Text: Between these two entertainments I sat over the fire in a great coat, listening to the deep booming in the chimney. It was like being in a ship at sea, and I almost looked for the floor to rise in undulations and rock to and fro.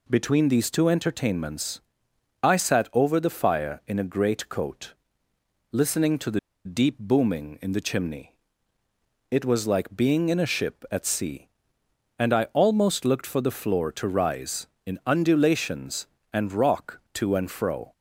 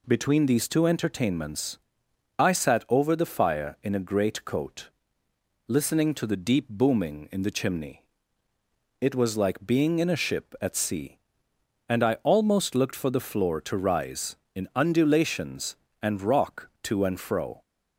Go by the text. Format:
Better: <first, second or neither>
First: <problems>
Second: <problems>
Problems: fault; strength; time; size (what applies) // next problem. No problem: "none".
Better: second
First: pauses between "entertainments" and "I"; noticeable; at 1.8 s; 0.60 s long // pauses between "the" and "deep"; slight; at 6.3 s; 0.26 s long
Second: pauses between "entertainments" and "I"; noticeable; at 1.7 s; 0.58 s long